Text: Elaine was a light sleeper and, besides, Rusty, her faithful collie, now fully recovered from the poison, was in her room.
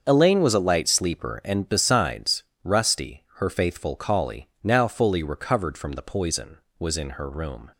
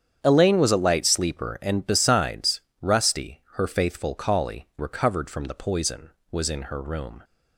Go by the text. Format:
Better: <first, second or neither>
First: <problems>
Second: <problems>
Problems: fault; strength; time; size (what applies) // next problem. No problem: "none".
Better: first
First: starts louder than the rest; until 1.0 s; 6.5 dB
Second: starts louder than the rest; strong; until 1.2 s; 8.5 dB // skips "now fully"; at 4.7 s